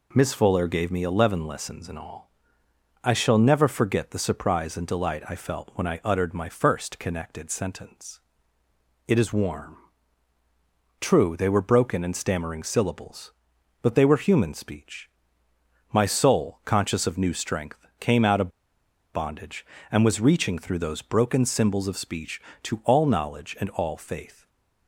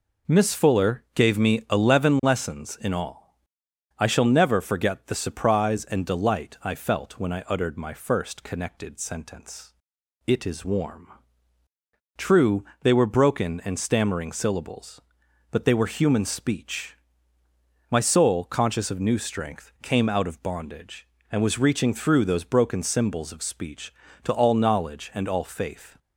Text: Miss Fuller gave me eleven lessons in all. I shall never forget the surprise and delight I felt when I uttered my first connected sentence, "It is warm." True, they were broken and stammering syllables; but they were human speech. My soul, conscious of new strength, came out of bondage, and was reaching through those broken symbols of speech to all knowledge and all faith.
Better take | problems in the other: second | pauses between "of" and "bondage"; noticeable; at 18.5 s; 0.63 s long // stays silent after the last word; slight; from 24.3 s on; 0.5 s long

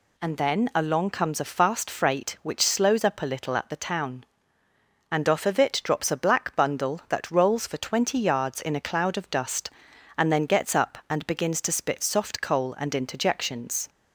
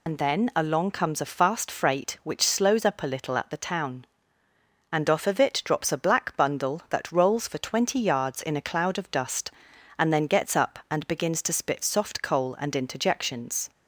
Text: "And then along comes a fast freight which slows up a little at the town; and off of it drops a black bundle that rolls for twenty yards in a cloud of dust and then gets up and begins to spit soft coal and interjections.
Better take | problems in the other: first | loses the start of "And"; at 0.0 s; 65 ms

